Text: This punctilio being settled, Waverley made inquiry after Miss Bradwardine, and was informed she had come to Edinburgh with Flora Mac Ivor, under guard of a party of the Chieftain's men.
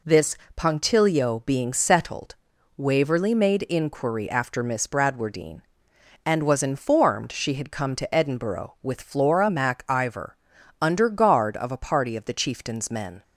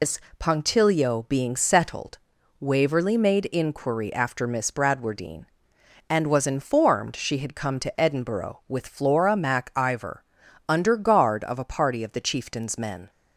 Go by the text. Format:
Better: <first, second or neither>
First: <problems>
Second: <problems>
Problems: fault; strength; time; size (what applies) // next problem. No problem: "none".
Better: first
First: pauses between "This" and "punctilio"; slight; at 0.3 s; 0.22 s long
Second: loses the start of "This"; at 0.0 s; 140 ms // pauses between "This" and "punctilio"; slight; at 0.1 s; 0.22 s long